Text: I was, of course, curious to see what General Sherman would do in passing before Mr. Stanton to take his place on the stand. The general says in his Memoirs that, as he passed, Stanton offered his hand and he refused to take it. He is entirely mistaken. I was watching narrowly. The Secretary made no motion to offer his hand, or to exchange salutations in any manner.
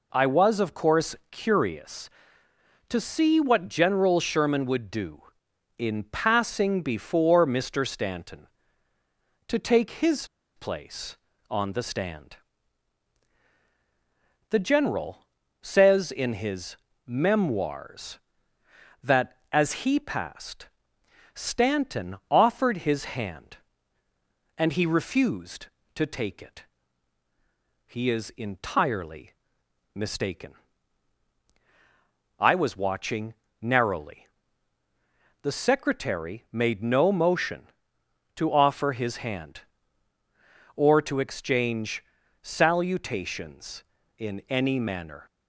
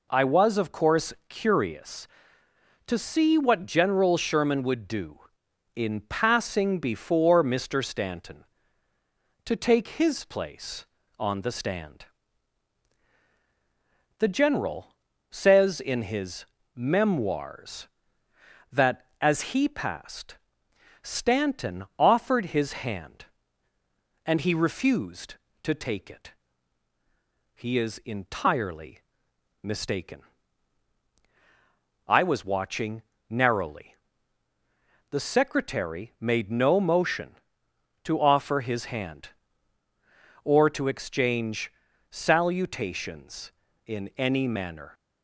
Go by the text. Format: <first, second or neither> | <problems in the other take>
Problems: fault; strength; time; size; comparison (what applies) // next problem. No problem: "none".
second | pauses between "his" and "place"; slight; at 10.2 s; 0.29 s long // pauses between "general" and "says"; slight; at 15.2 s; 0.36 s long; slight in the second // pauses between "his" and "Memoirs"; slight; at 16.7 s; 0.30 s long; slight in the second // pauses between "entirely" and "mistaken"; noticeable; at 29.3 s; 0.64 s long; noticeable in the second // pauses between "watching" and "narrowly"; slight; at 33.3 s; 0.26 s long; slight in the second // pauses between "exchange" and "salutations"; at 42.0 s; 0.40 s long; also in the second